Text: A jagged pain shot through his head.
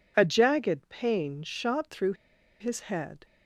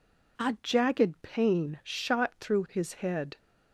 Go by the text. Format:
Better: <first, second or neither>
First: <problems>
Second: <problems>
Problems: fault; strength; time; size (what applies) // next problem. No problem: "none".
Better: second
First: pauses between "through" and "his"; noticeable; at 2.1 s; 0.46 s long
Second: none